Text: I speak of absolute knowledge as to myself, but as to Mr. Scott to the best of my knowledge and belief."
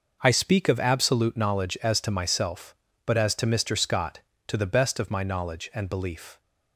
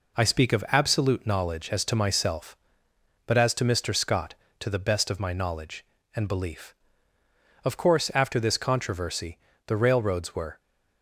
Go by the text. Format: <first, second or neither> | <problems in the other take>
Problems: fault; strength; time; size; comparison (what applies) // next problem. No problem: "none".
first | goes on to say "Of course after this controversy the railroads were"; strong; from 7.6 s on; 2.9 s long